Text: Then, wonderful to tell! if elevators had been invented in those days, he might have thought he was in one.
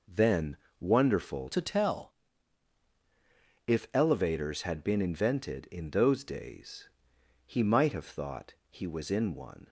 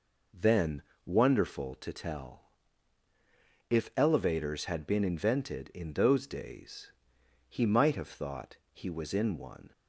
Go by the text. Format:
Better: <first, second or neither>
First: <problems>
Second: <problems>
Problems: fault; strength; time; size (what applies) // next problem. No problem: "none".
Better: second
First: changes voice from "to" to "tell"; from 1.5 to 2.1 s; 0.6 s long // pauses between "thought" and "he"; slight; at 8.5 s; 0.18 s long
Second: pauses between "thought" and "he"; slight; at 8.5 s; 0.18 s long